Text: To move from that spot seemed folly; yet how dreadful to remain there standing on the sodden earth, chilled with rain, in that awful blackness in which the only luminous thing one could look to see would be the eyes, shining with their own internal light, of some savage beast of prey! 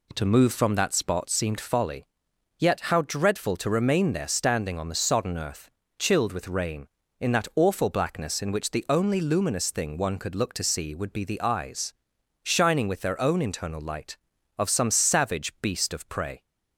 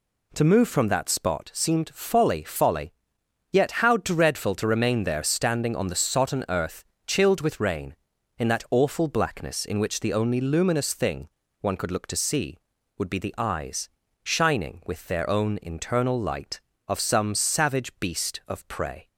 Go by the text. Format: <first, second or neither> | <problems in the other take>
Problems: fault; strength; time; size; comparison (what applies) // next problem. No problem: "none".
first | says "folly" twice; at 2.4 s // pauses between "thing" and "one"; slight; at 11.2 s; 0.32 s long